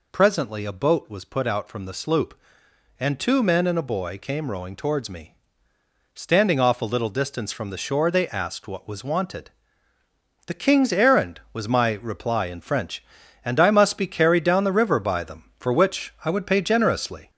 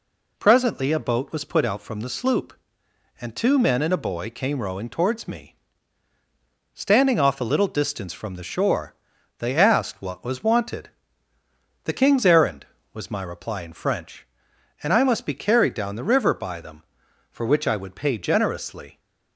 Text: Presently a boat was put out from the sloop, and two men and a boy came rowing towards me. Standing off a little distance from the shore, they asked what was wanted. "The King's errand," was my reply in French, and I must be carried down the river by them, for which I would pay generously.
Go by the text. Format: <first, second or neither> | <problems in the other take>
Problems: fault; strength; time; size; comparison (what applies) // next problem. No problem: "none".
second | gets louder; noticeable; throughout; 4.5 dB